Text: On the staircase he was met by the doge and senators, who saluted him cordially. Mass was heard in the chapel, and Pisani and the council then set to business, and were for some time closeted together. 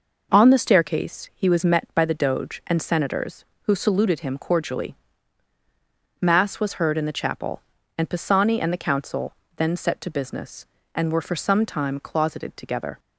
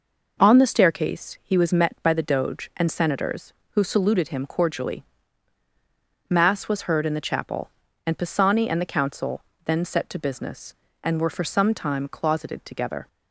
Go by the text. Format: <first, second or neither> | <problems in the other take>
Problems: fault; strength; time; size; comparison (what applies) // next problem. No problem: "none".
neither | pauses between "council" and "then"; slight; the same in both